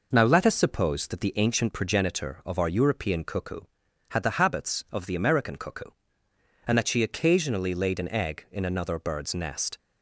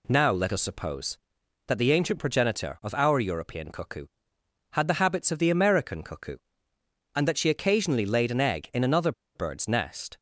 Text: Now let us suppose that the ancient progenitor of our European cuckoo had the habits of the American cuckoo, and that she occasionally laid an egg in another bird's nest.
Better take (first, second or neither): first